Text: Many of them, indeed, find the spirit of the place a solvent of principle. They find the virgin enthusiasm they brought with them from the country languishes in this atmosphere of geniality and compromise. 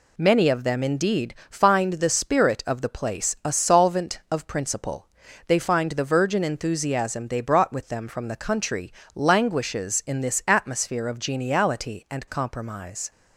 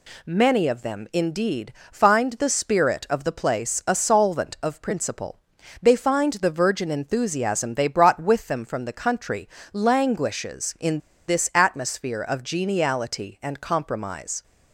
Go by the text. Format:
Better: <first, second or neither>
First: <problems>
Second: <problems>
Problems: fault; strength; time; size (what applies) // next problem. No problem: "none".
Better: first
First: pauses between "country" and "languishes"; slight; at 8.9 s; 0.24 s long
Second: pauses between "country" and "languishes"; slight; at 9.4 s; 0.24 s long // pauses between "in" and "this"; slight; at 10.9 s; 0.28 s long